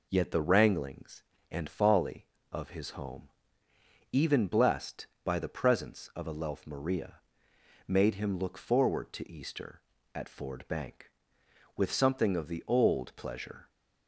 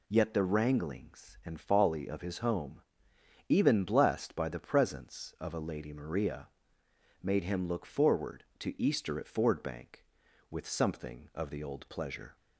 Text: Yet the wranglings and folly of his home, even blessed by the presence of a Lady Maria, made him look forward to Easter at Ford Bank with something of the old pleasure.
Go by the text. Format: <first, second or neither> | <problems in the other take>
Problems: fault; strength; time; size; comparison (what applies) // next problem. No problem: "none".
second | says "Lelf" for "Lady"; at 6.3 s